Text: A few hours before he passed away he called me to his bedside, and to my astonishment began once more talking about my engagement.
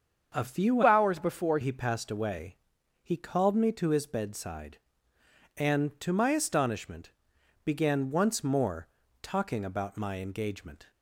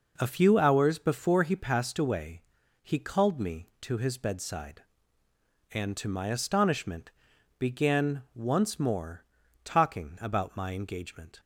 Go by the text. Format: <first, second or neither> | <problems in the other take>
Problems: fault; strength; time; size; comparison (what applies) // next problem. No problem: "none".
second | starts louder than the rest; until 1.4 s; 6.5 dB // changes voice from "hours" to "before"; from 0.8 to 1.5 s; 0.7 s long // pauses between "away" and "he"; noticeable; at 2.5 s; 0.48 s long; also in the second // pauses between "astonishment" and "began"; noticeable; at 7.1 s; 0.54 s long; noticeable in the second // pauses between "more" and "talking"; slight; at 8.8 s; 0.36 s long; also in the second